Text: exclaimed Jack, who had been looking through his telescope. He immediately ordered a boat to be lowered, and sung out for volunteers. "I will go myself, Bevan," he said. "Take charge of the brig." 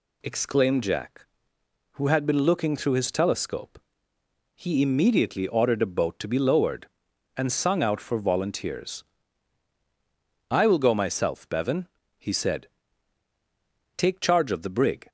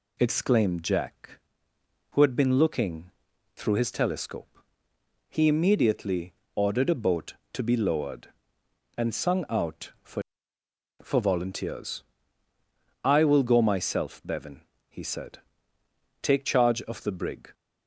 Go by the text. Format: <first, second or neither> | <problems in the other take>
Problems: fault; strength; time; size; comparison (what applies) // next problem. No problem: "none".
first | pauses between "looking" and "through"; at 3.1 s; 0.44 s long // pauses between "immediately" and "ordered"; slight; at 6.3 s; 0.22 s long // says "for" twice; at 11.0 s